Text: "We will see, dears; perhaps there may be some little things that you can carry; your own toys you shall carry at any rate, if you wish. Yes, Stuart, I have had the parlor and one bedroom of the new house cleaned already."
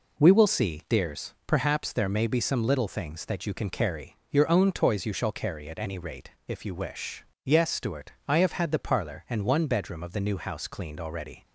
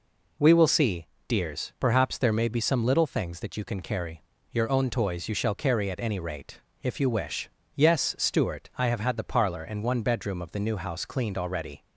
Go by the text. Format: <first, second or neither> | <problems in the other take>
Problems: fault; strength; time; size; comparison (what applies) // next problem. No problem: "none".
neither | none